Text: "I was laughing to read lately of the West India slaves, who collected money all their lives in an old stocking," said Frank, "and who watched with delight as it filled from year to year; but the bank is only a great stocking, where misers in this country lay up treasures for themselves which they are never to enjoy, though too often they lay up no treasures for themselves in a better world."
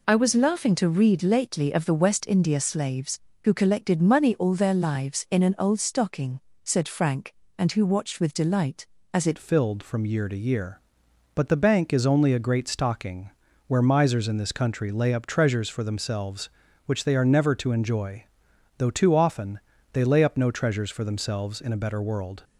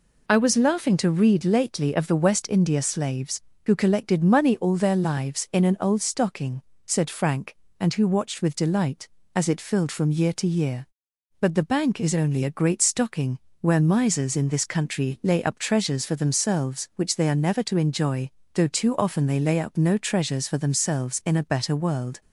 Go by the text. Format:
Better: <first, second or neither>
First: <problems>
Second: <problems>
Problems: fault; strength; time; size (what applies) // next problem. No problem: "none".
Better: second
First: changes voice at "filled"; from 9.3 s on; 13.1 s long // pauses between "often" and "they"; slight; at 19.5 s; 0.32 s long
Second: none